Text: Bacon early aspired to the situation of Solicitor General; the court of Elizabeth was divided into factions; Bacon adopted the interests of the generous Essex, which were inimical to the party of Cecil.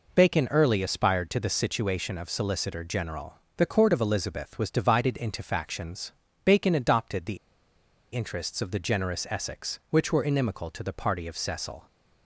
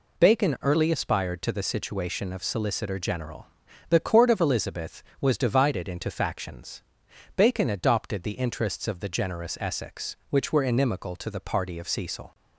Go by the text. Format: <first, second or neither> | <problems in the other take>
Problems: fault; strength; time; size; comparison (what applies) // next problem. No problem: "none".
second | pauses between "the" and "interests"; noticeable; at 7.3 s; 0.76 s long